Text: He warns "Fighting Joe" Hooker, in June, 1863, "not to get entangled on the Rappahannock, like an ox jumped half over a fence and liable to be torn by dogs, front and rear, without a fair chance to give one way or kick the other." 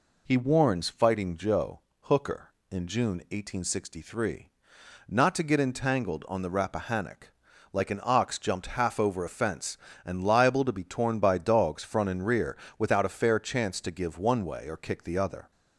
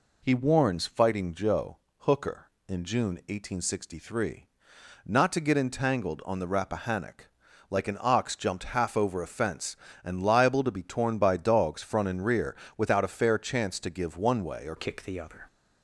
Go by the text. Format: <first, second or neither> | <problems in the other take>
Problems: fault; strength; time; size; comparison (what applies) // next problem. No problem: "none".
first | pauses between "Joe" and "Hooker"; slight; at 1.7 s; 0.22 s long; slight in the first // changes voice at "kick"; from 14.7 s on; 0.7 s long